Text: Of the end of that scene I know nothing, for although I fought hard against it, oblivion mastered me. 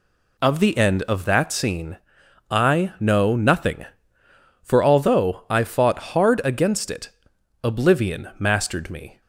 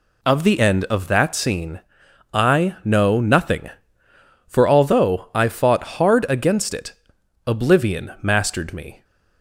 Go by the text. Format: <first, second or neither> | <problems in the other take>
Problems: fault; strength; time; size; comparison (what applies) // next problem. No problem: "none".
neither | pauses between "scene" and "I"; noticeable; the same in both